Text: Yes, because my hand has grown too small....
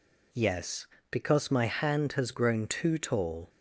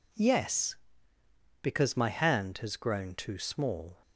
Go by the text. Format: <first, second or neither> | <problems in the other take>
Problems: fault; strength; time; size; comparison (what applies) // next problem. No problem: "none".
second | says "tall" for "small"; at 2.9 s